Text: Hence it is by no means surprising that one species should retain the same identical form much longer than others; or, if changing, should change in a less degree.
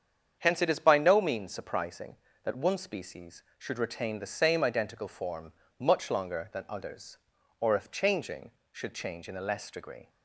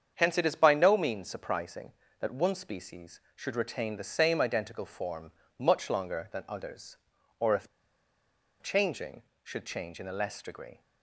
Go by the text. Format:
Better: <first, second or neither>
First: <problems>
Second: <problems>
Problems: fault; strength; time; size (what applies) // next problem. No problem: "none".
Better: first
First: starts louder than the rest; strong; until 1.4 s; 7.5 dB // pauses between "form" and "much"; slight; at 5.5 s; 0.26 s long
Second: starts louder than the rest; strong; until 1.1 s; 7.5 dB // pauses between "form" and "much"; slight; at 5.3 s; 0.26 s long // pauses between "if" and "changing"; noticeable; at 7.6 s; 0.94 s long